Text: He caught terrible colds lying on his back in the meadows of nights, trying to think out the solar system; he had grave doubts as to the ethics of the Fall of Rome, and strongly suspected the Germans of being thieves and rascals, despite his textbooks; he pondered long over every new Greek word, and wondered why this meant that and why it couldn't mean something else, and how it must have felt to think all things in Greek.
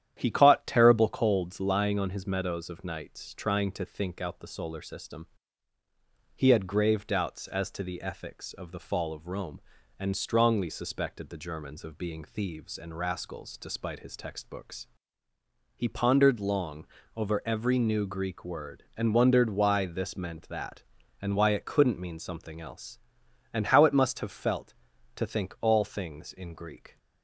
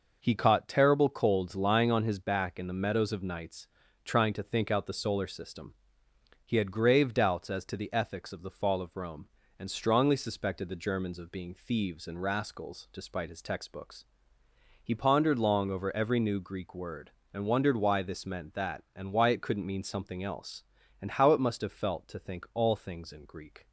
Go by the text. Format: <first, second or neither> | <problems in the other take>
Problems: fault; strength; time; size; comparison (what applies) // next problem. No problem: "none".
second | starts louder than the rest; strong; until 1.1 s; 10.5 dB // skips "back in the"; at 2.2 s // pauses between "long" and "over"; slight; at 16.8 s; 0.28 s long